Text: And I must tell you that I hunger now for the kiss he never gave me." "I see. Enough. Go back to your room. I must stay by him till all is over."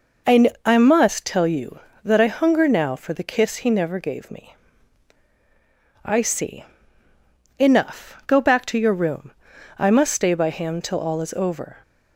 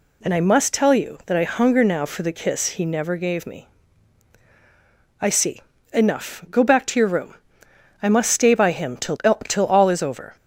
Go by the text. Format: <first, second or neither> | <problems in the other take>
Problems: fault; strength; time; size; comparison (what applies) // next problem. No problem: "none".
first | says "till" twice; at 9.4 s